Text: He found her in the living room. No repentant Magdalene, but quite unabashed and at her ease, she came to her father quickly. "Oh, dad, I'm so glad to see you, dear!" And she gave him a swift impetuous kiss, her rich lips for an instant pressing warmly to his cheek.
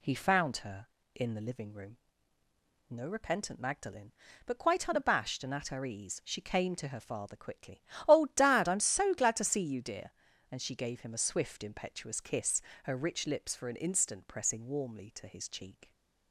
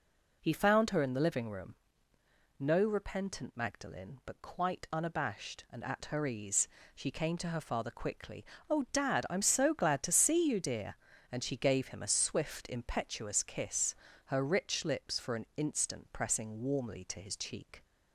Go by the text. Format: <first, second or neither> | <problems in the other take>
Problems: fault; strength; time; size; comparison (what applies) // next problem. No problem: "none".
neither | none